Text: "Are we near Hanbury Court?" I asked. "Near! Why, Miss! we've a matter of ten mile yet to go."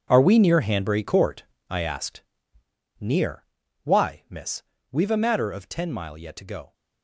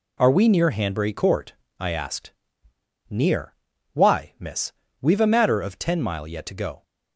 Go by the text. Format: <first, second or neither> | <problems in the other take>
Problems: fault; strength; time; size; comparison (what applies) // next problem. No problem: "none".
second | gets quieter; strong; throughout; 13.5 dB